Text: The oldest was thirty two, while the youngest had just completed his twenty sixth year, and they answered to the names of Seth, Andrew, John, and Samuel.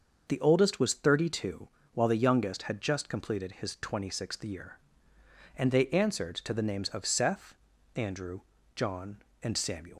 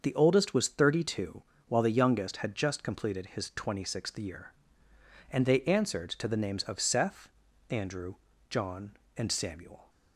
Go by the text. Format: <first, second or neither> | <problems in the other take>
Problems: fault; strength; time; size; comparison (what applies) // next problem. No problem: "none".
second | starts louder than the rest; until 1.2 s; 6.5 dB; also in the second // leaves "Samuel" unfinished; at 9.9 s; 165 ms